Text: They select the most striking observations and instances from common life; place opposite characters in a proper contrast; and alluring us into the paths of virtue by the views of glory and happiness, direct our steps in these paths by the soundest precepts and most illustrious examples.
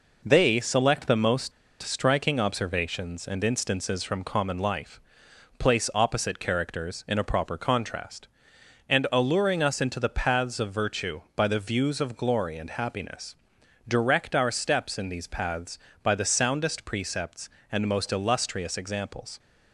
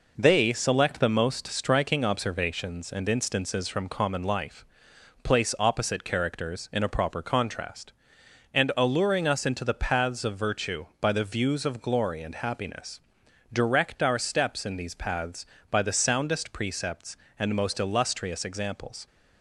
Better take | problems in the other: second | pauses between "most" and "striking"; slight; at 1.5 s; 0.30 s long

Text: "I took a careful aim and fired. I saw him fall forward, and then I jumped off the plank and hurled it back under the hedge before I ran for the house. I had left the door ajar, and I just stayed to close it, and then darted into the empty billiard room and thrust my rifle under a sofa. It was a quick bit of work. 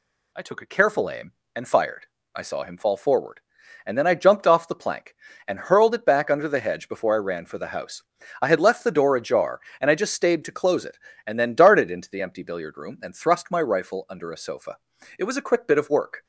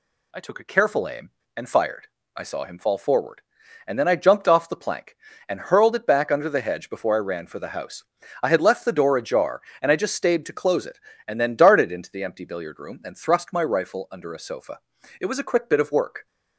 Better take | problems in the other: neither | none

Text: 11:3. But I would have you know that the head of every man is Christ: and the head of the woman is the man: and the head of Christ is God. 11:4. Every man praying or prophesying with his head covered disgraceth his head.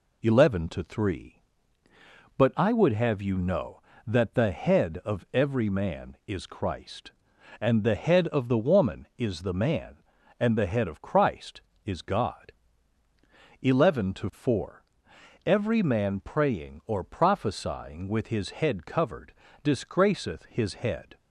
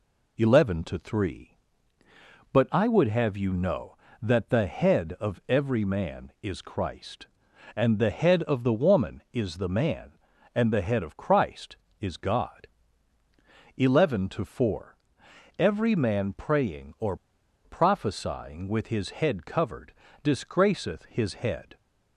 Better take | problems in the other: first | pauses between "or" and "prophesying"; noticeable; at 17.1 s; 0.50 s long // pauses between "covered" and "disgraceth"; slight; at 19.9 s; 0.32 s long; slight in the first

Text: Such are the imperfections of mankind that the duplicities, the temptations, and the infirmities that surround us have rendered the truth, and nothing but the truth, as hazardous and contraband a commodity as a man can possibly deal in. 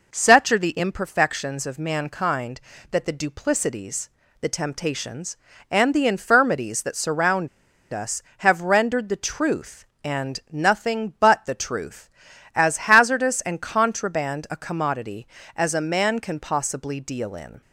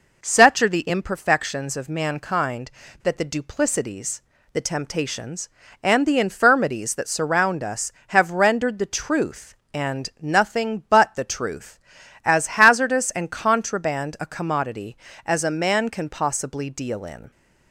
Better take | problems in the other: second | pauses between "surround" and "us"; at 7.4 s; 0.44 s long

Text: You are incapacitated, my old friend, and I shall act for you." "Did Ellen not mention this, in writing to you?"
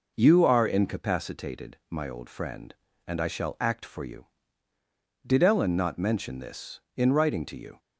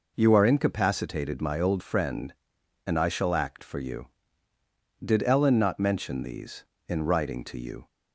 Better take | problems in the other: first | says "these" for "this"; at 6.2 s

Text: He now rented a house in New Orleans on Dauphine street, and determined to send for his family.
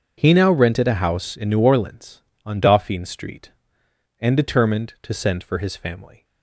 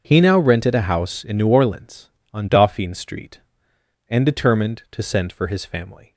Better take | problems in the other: neither | starts louder than the rest; the same in both

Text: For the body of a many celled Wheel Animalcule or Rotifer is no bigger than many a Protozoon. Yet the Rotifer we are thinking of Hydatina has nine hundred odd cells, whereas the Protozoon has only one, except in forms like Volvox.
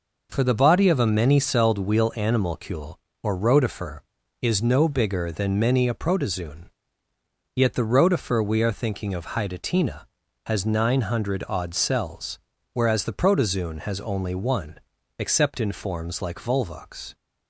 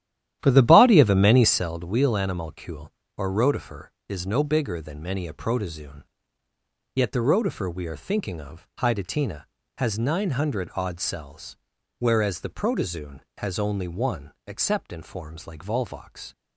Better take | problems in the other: first | starts louder than the rest; strong; until 1.7 s; 11.5 dB

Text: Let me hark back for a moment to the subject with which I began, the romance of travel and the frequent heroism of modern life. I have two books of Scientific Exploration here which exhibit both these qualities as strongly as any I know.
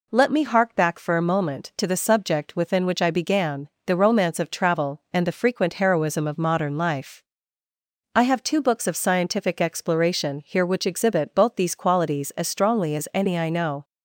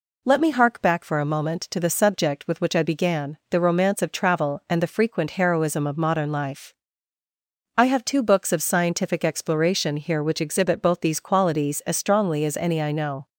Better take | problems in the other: second | says "within" for "with"; at 2.5 s

